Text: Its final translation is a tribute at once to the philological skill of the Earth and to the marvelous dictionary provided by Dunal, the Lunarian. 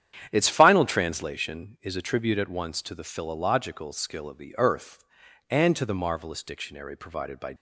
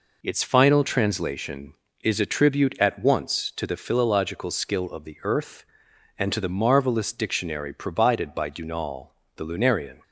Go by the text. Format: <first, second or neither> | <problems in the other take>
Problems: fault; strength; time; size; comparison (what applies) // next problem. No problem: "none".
second | starts louder than the rest; strong; until 1.3 s; 9.5 dB // stops before "Dunal the Lunarian"; at 7.5 s